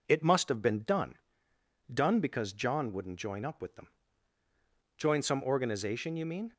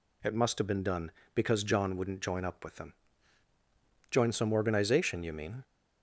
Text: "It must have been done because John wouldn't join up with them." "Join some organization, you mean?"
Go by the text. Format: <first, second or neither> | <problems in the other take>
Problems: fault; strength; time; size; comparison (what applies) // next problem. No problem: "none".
second | says "done" twice; at 1.9 s